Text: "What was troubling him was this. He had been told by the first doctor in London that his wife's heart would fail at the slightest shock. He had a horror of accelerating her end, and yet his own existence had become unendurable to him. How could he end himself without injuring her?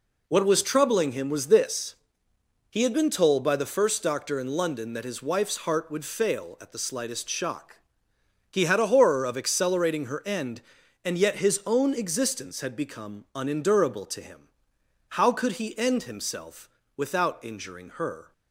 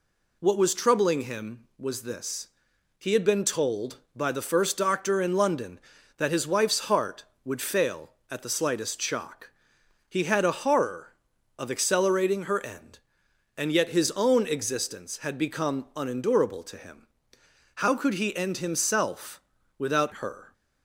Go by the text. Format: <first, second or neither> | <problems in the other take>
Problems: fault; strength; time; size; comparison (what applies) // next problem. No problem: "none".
first | pauses between "himself" and "without"; slight; at 19.4 s; 0.36 s long; slight in the first // skips "injuring"; at 20.1 s